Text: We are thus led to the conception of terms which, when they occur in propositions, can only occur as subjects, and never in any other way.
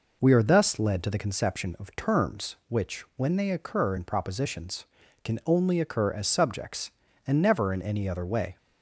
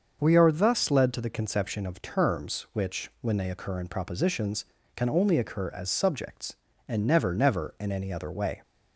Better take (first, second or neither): first